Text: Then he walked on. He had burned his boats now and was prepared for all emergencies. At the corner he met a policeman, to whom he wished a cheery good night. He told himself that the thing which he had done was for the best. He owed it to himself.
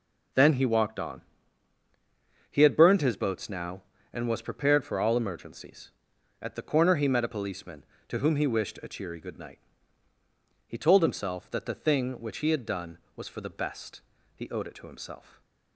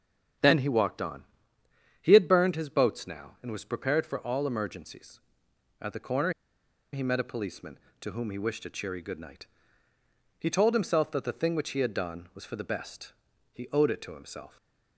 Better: first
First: stays silent after the last word; slight; from 15.1 s on; 0.6 s long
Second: starts louder than the rest; strong; until 2.1 s; 8 dB // pauses between "corner" and "he"; noticeable; at 6.3 s; 0.60 s long // stays silent after the last word; slight; from 14.4 s on; 0.5 s long

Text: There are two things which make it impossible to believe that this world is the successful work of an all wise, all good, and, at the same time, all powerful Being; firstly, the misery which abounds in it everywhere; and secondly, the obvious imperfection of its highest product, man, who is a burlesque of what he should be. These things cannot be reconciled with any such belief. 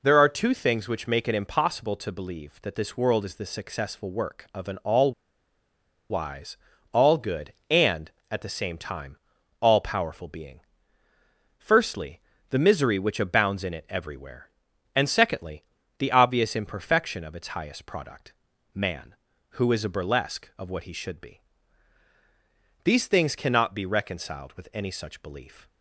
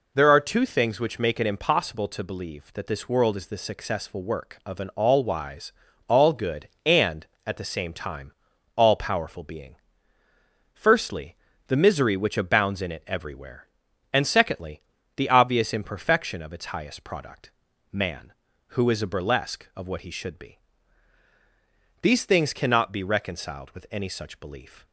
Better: second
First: pauses between "all" and "wise"; at 5.1 s; 0.99 s long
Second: none

